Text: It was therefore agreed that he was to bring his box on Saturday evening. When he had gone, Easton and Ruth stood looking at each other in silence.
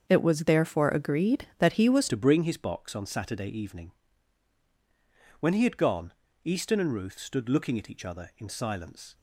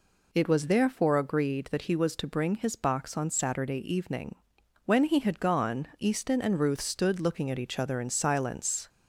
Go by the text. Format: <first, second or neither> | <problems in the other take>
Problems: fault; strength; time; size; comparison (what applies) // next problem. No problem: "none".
second | starts louder than the rest; until 1.0 s; 7 dB // changes voice at "to"; from 2.0 s on; 7.1 s long